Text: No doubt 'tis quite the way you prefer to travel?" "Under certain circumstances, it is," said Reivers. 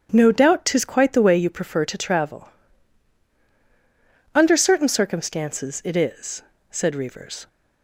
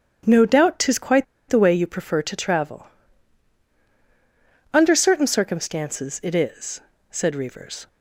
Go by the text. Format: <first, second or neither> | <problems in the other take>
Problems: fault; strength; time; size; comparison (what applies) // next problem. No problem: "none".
first | starts louder than the rest; strong; until 1.5 s; 9 dB; strong in the first // pauses between "quite" and "the"; slight; at 1.2 s; 0.24 s long